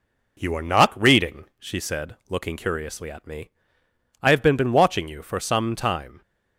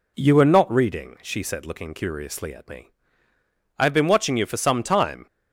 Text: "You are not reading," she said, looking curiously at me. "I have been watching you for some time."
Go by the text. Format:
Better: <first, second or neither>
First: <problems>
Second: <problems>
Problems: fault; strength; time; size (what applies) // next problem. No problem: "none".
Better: second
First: says "been" twice; at 4.5 s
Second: none